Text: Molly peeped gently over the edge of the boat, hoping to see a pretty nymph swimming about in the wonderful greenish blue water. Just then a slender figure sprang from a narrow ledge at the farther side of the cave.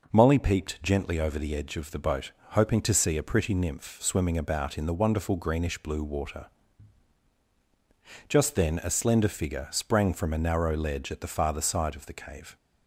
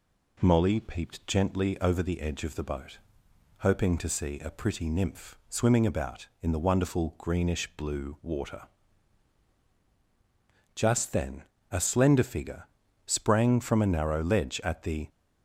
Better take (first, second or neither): first